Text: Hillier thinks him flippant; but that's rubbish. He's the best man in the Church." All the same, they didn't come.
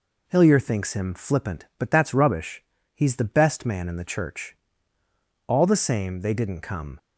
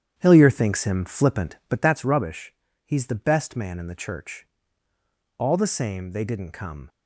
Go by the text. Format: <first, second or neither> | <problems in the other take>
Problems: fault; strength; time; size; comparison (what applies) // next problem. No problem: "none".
first | starts louder than the rest; strong; until 2.0 s; 9.5 dB